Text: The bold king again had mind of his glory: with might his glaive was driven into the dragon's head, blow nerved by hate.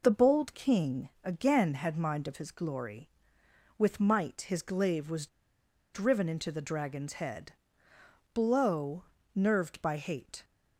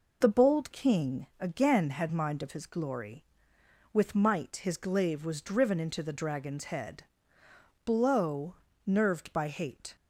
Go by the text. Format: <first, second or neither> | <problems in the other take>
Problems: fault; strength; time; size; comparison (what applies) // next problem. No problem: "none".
second | pauses between "king" and "again"; slight; at 1.0 s; 0.16 s long // pauses between "was" and "driven"; noticeable; at 5.2 s; 0.66 s long // pauses between "blow" and "nerved"; slight; at 9.0 s; 0.30 s long; slight in the second